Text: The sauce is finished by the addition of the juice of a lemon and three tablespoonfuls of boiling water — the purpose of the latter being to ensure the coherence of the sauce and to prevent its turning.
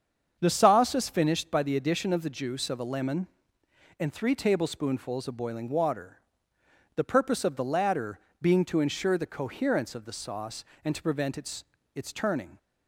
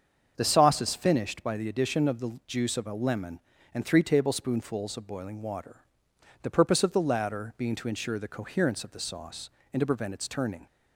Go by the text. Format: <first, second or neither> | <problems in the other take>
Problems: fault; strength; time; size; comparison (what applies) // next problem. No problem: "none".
second | starts louder than the rest; strong; until 1.4 s; 7 dB; also in the second // pauses between "latter" and "being"; slight; at 8.1 s; 0.20 s long // says "its" twice; at 11.9 s